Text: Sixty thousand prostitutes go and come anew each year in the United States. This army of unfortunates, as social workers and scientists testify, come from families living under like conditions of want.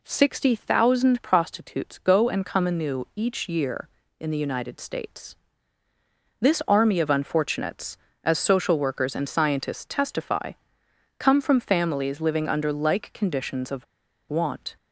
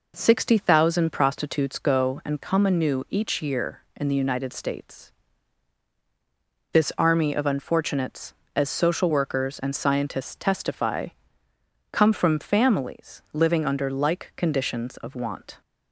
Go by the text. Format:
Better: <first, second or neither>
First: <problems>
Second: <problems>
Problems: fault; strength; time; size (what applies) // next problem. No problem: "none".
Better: second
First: pauses between "of" and "want"; at 13.8 s; 0.44 s long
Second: none